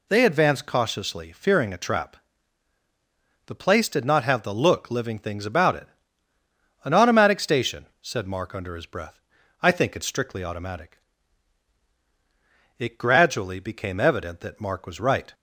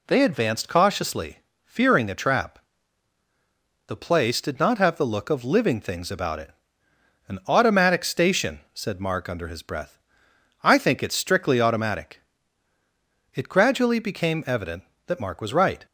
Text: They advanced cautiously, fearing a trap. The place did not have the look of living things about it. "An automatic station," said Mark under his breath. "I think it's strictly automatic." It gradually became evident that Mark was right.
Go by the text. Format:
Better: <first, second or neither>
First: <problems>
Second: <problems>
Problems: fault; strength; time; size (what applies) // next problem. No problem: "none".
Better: second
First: skips "of"; at 4.8 s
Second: none